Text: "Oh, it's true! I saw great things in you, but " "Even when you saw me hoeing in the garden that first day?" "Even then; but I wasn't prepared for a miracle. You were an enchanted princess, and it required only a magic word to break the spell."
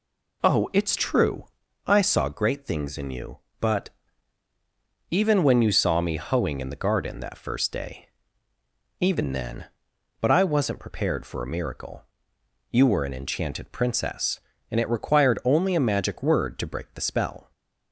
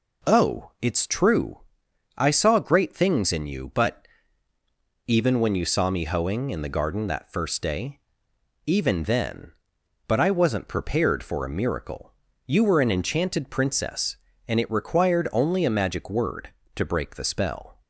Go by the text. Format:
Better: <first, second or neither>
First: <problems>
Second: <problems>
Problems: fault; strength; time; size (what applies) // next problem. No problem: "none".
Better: neither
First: none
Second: none